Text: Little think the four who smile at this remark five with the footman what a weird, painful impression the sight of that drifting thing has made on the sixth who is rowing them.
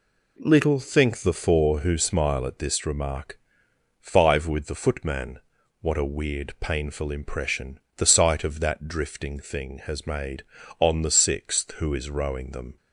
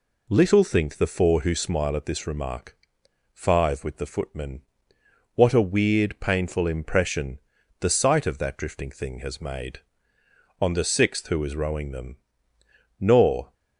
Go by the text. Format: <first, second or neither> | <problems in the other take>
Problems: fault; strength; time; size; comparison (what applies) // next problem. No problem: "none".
first | pauses between "remark" and "five"; noticeable; at 2.7 s; 0.56 s long; noticeable in the first // pauses between "footman" and "what"; noticeable; at 4.6 s; 0.74 s long; also in the first // pauses between "impression" and "the"; at 7.3 s; 0.42 s long; slight in the first // goes on to say "Nor"; from 13.0 s on; 0.52 s long